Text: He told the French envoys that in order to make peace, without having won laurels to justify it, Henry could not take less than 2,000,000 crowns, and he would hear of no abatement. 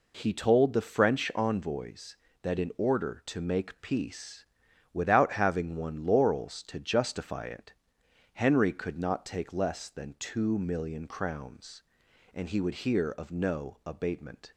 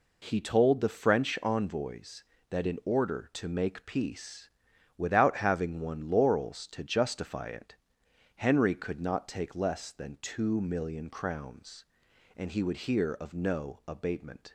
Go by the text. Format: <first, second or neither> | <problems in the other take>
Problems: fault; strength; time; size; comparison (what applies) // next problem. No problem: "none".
neither | none